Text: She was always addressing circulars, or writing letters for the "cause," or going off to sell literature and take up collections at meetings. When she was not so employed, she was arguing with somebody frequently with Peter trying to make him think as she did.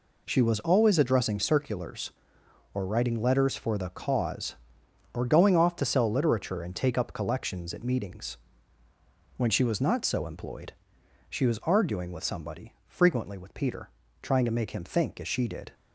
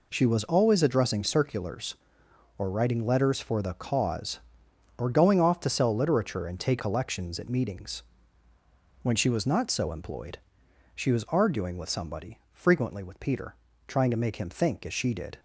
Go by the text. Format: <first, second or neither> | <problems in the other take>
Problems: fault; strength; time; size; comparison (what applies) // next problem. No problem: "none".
first | skips "up"; at 6.7 s // pauses between "Peter" and "trying"; slight; at 13.5 s; 0.32 s long; slight in the first